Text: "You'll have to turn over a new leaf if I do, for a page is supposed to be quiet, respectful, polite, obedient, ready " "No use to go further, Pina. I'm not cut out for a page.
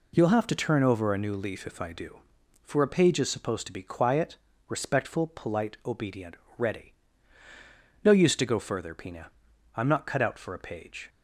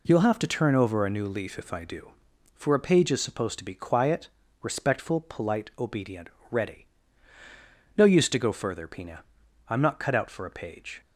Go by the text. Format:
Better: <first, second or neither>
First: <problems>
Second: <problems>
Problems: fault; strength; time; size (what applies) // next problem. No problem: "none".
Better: neither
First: none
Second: none